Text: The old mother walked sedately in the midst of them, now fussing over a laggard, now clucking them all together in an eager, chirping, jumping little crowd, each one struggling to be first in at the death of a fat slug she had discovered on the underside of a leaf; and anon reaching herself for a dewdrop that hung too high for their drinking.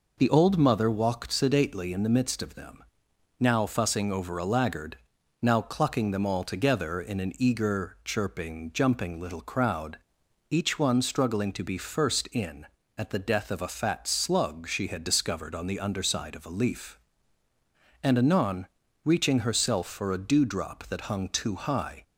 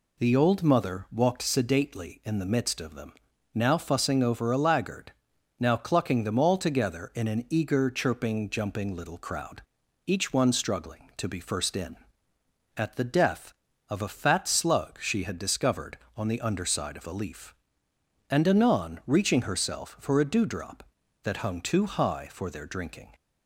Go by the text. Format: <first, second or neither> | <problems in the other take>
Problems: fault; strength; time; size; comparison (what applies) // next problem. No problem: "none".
second | pauses between "anon" and "reaching"; at 18.6 s; 0.38 s long // stops before "for their drinking"; at 22.0 s